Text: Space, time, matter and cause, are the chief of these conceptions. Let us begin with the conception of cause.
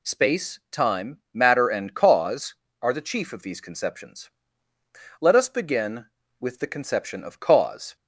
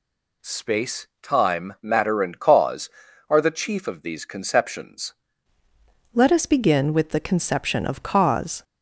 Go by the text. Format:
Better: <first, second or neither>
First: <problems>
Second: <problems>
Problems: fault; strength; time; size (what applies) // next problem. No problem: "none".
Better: first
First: none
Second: changes voice at "Let"; from 6.1 s on; 2.5 s long